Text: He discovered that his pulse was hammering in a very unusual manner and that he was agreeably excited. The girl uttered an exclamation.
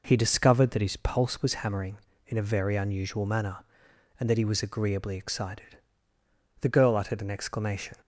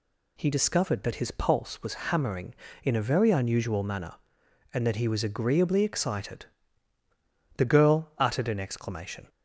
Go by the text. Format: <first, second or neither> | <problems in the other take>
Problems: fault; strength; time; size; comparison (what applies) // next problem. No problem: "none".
neither | none